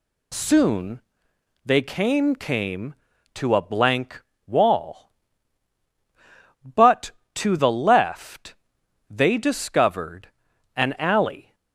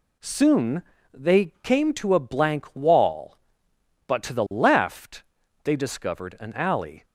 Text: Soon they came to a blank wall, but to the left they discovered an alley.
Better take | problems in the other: second | pauses between "Soon" and "they"; noticeable; at 0.9 s; 0.64 s long; slight in the second // says "came" twice; at 2.3 s // pauses between "blank" and "wall"; slight; at 4.2 s; 0.26 s long // pauses between "left" and "they"; noticeable; at 8.5 s; 0.56 s long; also in the second // pauses between "discovered" and "an"; noticeable; at 10.2 s; 0.48 s long

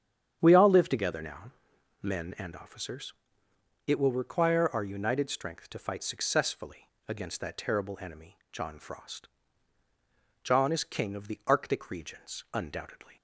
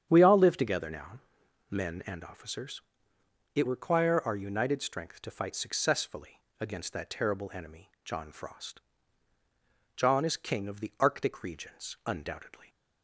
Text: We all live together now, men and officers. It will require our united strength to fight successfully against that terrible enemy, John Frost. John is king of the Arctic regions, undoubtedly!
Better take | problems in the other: first | starts louder than the rest; strong; until 1.1 s; 9 dB; strong in the first // skips "will"; at 3.6 s // pauses between "successfully" and "against"; slight; at 6.4 s; 0.18 s long; slight in the first

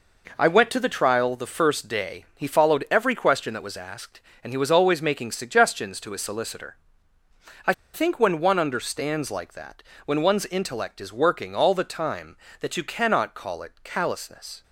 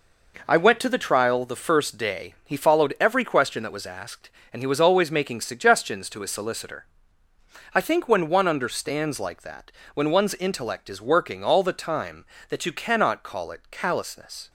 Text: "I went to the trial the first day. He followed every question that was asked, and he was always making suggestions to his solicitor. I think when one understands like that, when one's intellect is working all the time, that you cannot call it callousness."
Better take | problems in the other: second | pauses between "I" and "think"; slight; at 7.7 s; 0.20 s long

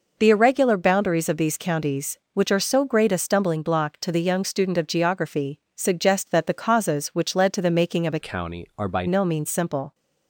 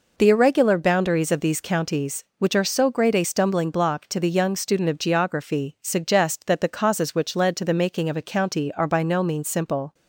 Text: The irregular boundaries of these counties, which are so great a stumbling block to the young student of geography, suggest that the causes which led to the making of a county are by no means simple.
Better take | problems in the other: second | changes voice from "county" to "by"; from 8.2 to 9.0 s; 0.8 s long

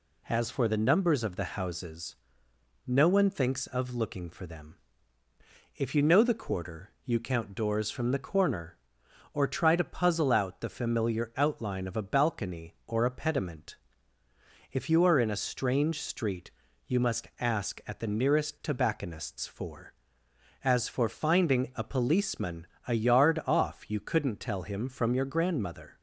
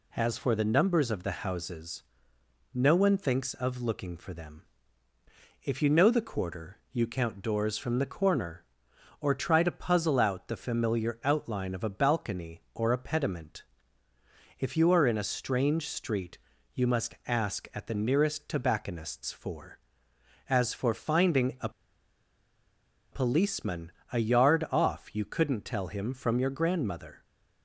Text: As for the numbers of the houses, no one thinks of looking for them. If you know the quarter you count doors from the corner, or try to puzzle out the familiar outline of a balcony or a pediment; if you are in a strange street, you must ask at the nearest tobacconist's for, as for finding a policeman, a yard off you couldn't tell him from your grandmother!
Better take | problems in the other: first | pauses between "a" and "policeman"; strong; at 21.6 s; 1.4 s long

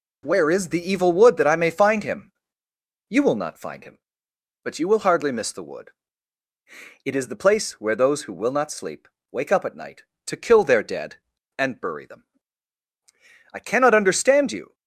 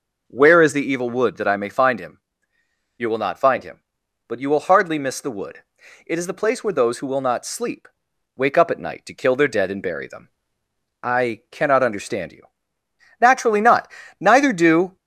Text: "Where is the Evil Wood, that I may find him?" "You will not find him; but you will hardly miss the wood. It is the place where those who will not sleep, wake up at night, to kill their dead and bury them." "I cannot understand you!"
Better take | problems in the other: first | goes on to say "Naturally not Neither do"; strong; from 13.2 s on; 1.7 s long

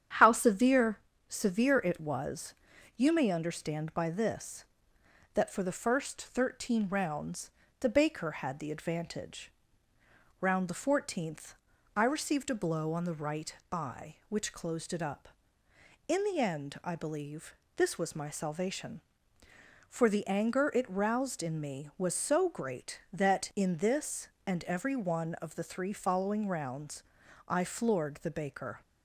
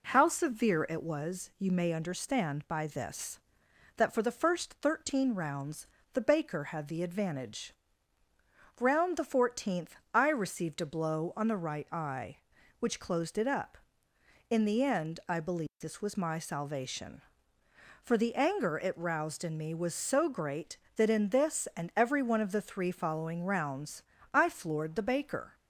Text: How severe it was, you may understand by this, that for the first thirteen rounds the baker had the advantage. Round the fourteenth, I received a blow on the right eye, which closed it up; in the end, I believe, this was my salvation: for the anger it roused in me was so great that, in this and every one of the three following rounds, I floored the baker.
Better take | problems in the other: second | starts louder than the rest; strong; until 1.4 s; 9.5 dB // says "severe" twice; at 1.2 s // pauses between "rounds" and "the"; slight; at 7.4 s; 0.30 s long; slight in the second // pauses between "right" and "eye"; slight; at 13.5 s; 0.16 s long

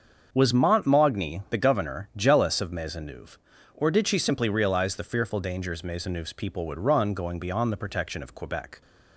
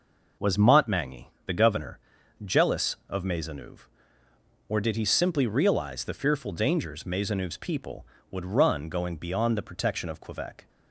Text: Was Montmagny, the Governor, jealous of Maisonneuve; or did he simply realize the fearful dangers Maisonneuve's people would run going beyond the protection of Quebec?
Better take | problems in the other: second | starts louder than the rest; until 1.3 s; 7 dB // says "she" for "he"; at 4.0 s

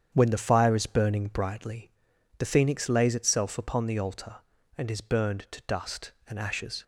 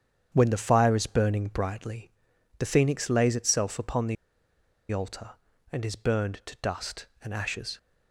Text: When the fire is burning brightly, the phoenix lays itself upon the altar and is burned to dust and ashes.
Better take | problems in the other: first | starts louder than the rest; strong; until 1.3 s; 8.5 dB; strong in the first // pauses between "the" and "altar"; noticeable; at 4.1 s; 0.76 s long

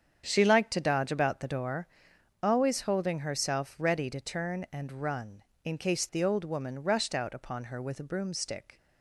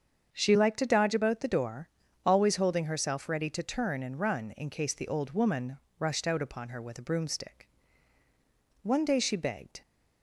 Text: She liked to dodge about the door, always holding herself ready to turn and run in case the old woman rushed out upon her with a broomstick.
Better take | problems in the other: first | starts louder than the rest; strong; until 1.3 s; 7 dB; strong in the first // pauses between "woman" and "rushed"; slight; at 5.7 s; 0.20 s long // goes on to say "One day she begged"; noticeable; from 8.8 s on; 0.98 s long

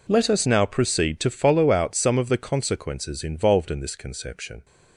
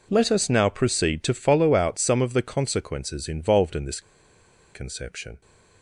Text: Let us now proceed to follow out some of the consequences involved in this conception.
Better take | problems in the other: first | pauses between "this" and "conception"; noticeable; at 3.9 s; 0.73 s long

